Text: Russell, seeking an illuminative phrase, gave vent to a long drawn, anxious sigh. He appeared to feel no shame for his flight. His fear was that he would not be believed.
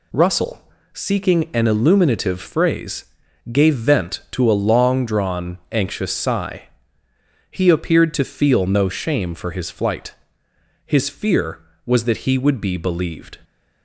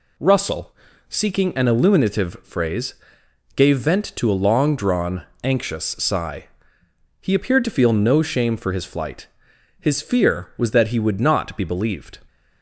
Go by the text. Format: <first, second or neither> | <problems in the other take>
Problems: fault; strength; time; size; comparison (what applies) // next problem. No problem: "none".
second | skips "not"; at 12.5 s